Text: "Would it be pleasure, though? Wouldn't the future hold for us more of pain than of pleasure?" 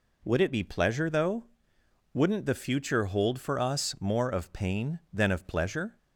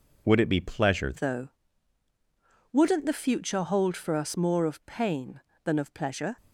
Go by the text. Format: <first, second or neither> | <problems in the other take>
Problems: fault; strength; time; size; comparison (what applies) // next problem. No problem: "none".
first | changes voice at "though"; from 1.1 s on; 5.2 s long